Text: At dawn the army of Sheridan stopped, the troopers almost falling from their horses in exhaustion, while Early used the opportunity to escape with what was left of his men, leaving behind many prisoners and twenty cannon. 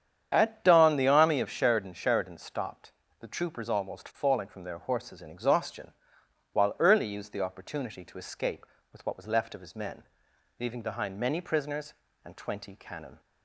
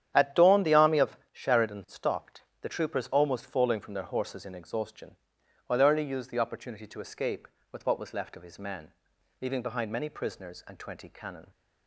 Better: second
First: starts louder than the rest; strong; until 1.3 s; 8.5 dB // says "Sheridan" twice; at 1.9 s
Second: starts louder than the rest; strong; until 1.1 s; 10 dB

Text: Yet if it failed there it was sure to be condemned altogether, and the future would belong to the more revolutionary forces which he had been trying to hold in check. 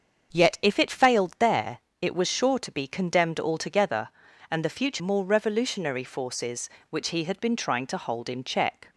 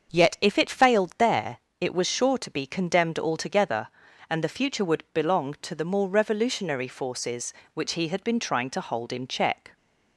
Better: second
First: starts louder than the rest; until 1.4 s; 7 dB // pauses between "there" and "it"; slight; at 1.7 s; 0.20 s long // skips "would belong to the"; at 5.0 s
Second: starts louder than the rest; until 1.2 s; 6.5 dB // pauses between "there" and "it"; slight; at 1.5 s; 0.20 s long

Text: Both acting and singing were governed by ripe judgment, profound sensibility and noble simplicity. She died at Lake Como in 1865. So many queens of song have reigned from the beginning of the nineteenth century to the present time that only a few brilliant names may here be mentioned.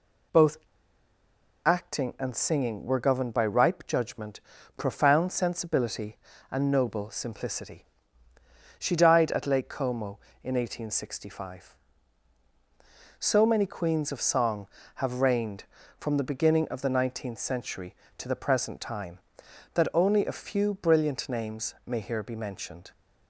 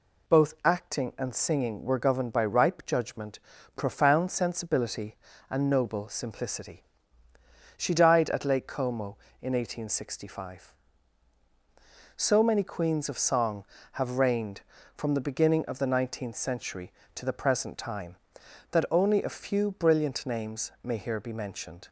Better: second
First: pauses between "Both" and "acting"; at 0.5 s; 1.0 s long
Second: none

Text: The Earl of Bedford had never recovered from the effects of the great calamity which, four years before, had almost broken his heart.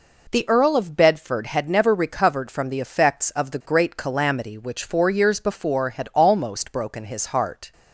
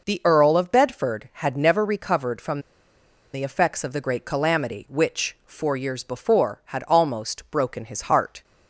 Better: first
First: none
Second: pauses between "from" and "the"; noticeable; at 2.5 s; 0.74 s long

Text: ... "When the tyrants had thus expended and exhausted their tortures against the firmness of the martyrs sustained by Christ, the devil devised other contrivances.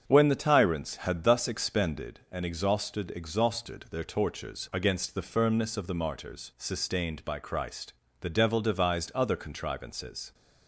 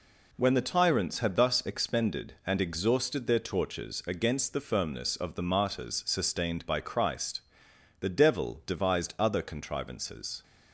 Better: second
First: starts louder than the rest; strong; until 1.0 s; 7.5 dB // says "exhausted" twice; at 3.1 s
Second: none

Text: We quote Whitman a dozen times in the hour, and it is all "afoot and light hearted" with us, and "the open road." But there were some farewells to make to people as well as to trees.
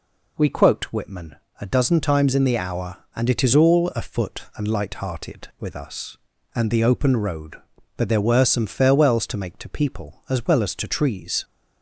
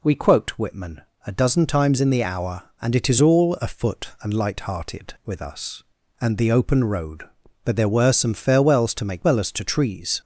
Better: first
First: pauses between "Whitman" and "a"; slight; at 1.3 s; 0.26 s long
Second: pauses between "Whitman" and "a"; slight; at 1.0 s; 0.26 s long // skips "to people as"; at 9.2 s

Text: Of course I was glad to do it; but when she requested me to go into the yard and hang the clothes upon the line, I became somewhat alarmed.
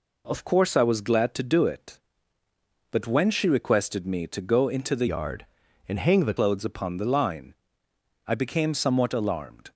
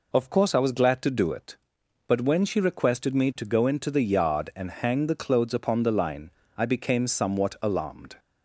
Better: second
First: changes voice from "yard" to "the"; from 5.0 to 6.3 s; 1.3 s long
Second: none

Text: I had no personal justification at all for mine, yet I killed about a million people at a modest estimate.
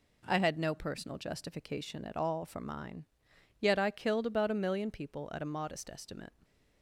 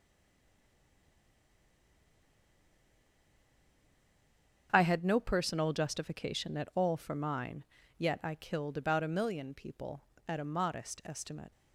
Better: first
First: none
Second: stays silent before the first word; strong; until 4.6 s; 4.6 s long // starts louder than the rest; strong; until 5.7 s; 7.5 dB

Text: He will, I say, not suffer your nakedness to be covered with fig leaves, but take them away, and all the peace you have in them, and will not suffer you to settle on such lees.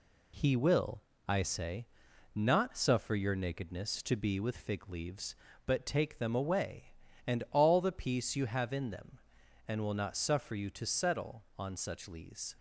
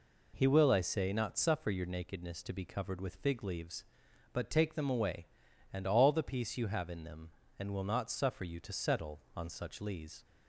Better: second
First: skips "covered"; at 4.4 s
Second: none

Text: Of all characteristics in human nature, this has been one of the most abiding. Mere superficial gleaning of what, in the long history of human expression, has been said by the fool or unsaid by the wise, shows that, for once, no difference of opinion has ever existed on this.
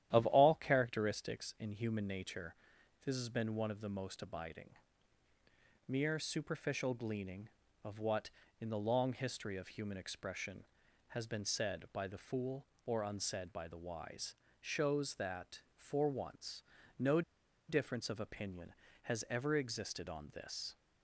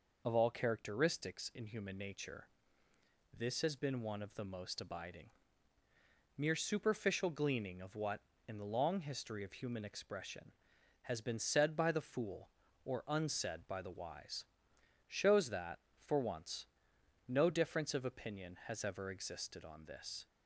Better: second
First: starts louder than the rest; strong; until 1.1 s; 11.5 dB // pauses between "no" and "difference"; noticeable; at 17.2 s; 0.47 s long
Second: none

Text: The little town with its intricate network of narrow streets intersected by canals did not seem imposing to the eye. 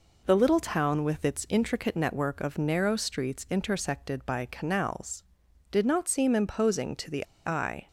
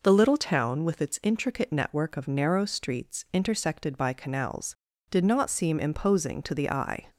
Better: second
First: pauses between "the" and "eye"; slight; at 7.2 s; 0.21 s long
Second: none

